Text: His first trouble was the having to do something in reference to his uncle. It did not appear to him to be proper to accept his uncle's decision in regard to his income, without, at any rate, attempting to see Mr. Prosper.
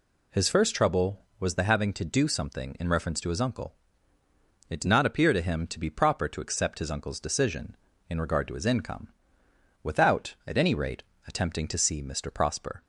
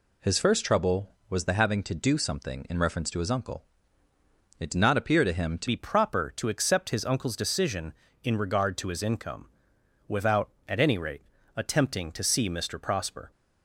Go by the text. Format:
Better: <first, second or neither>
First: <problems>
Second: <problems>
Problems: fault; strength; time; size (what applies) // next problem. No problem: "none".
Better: first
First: none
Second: changes voice at "be"; from 5.6 s on; 7.7 s long